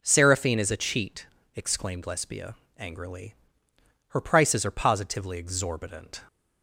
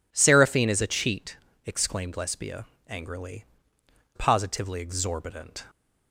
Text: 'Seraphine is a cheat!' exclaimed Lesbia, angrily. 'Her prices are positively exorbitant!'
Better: first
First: none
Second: skips "Her prices are"; at 3.7 s

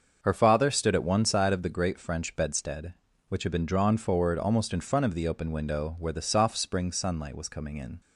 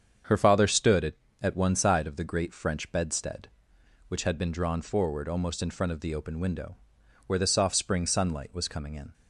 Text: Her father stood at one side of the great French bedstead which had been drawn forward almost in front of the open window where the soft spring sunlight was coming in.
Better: first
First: starts louder than the rest; until 1.2 s; 6.5 dB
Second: starts louder than the rest; strong; until 1.5 s; 7.5 dB // says "at" twice; at 1.4 s // pauses between "window" and "where"; noticeable; at 6.7 s; 0.48 s long

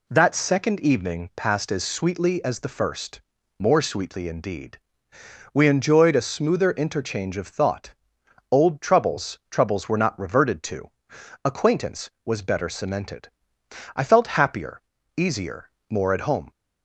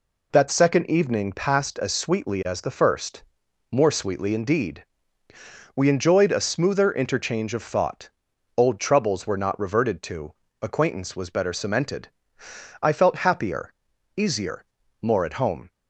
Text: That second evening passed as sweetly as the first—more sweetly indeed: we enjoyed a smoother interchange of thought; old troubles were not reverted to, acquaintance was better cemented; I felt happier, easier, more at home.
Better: second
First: says "troubles" twice; at 9.5 s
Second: none

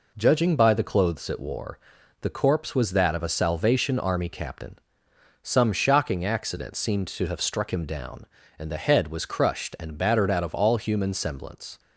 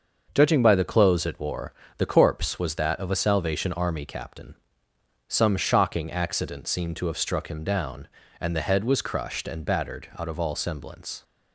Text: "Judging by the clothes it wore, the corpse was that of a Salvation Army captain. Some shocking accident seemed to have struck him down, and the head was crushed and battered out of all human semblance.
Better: first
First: none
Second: starts louder than the rest; until 1.3 s; 6.5 dB // skips "human"; at 10.5 s

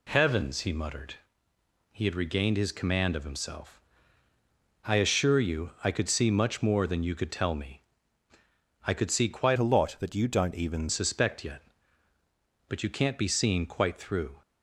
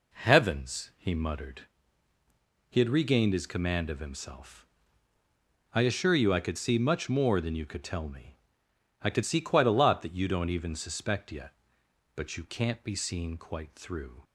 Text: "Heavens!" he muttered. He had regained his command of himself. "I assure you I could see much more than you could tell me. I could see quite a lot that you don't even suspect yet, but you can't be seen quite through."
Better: second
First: changes voice from "a" to "even"; from 9.5 to 10.8 s; 1.3 s long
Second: none

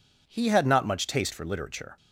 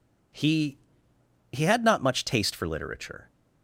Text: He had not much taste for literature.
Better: first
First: none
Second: says "He" twice; at 1.5 s

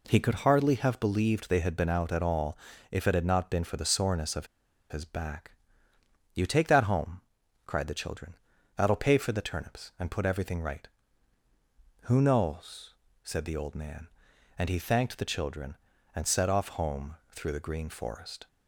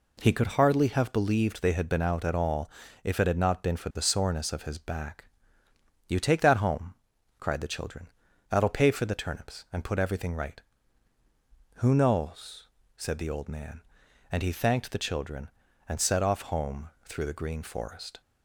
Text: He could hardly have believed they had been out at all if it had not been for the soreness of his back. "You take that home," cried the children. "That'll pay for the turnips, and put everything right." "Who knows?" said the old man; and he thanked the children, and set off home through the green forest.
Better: second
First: pauses between "all" and "if"; slight; at 2.5 s; 0.36 s long // pauses between "of" and "his"; at 4.4 s; 0.44 s long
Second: pauses between "all" and "if"; slight; at 2.6 s; 0.36 s long

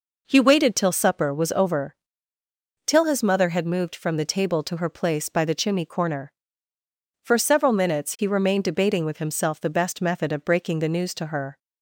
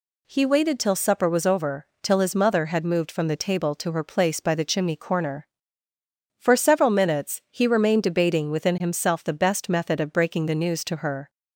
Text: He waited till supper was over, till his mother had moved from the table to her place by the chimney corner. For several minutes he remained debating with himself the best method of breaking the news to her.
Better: first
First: none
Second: says "within" for "with"; at 8.4 s

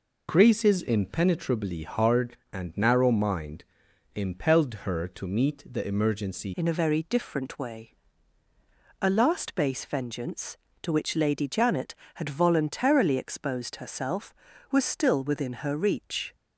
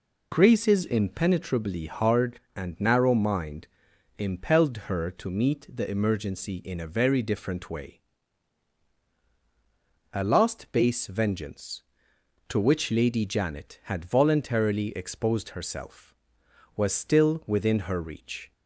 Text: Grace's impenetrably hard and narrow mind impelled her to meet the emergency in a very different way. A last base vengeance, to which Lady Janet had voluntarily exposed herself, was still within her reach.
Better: second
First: pauses between "mind" and "impelled"; noticeable; at 3.6 s; 0.50 s long // changes voice at "in"; from 6.5 s on; 9.8 s long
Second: pauses between "mind" and "impelled"; noticeable; at 3.6 s; 0.50 s long

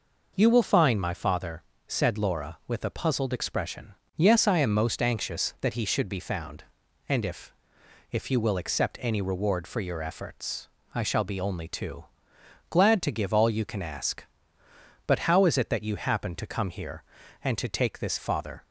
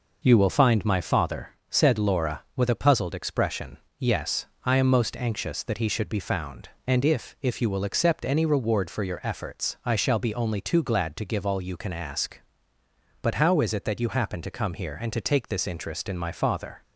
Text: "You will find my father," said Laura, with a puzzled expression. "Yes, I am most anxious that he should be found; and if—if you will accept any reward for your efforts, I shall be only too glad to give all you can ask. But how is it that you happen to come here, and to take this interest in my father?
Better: second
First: pauses between "too" and "glad"; noticeable; at 12.0 s; 0.66 s long // skips "interest in my"; at 18.1 s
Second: none

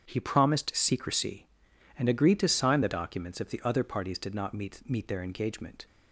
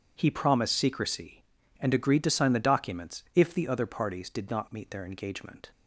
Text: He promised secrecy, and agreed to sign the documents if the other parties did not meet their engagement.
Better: second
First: starts louder than the rest; strong; until 1.0 s; 7.5 dB // says "meet" twice; at 4.8 s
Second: none

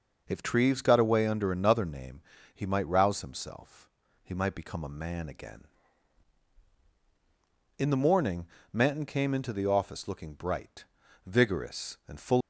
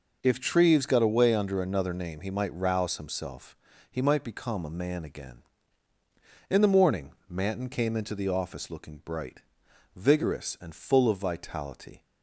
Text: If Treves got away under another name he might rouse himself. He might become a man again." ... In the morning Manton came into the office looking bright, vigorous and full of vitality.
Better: second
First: pauses between "name" and "he"; slight; at 2.2 s; 0.32 s long // pauses between "morning" and "Manton"; slight; at 8.4 s; 0.26 s long // stops before "of vitality"; at 12.4 s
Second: pauses between "morning" and "Manton"; slight; at 7.1 s; 0.16 s long

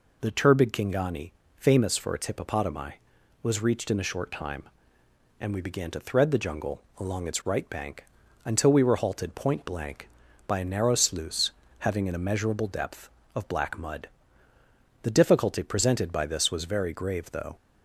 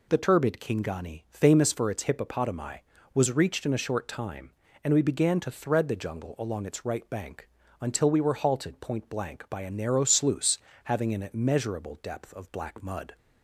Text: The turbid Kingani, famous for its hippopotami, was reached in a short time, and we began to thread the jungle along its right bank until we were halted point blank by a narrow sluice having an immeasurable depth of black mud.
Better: second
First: pauses between "jungle" and "along"; slight; at 6.8 s; 0.16 s long // pauses between "bank" and "until"; at 8.0 s; 0.38 s long // pauses between "sluice" and "having"; slight; at 11.5 s; 0.28 s long // goes on to say "The difficulty presented by this was very grave though"; strong; from 15.0 s on; 2.5 s long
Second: pauses between "bank" and "until"; slight; at 7.4 s; 0.32 s long // pauses between "sluice" and "having"; slight; at 10.5 s; 0.26 s long

